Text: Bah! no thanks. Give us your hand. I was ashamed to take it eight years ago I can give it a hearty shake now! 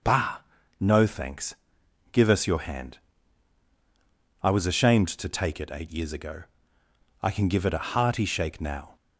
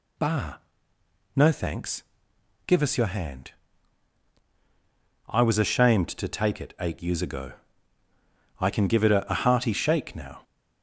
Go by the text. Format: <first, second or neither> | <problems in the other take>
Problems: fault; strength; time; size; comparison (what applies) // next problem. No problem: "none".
first | pauses between "ago" and "I"; at 7.5 s; 1.0 s long; noticeable in the first // says "a" twice; at 9.3 s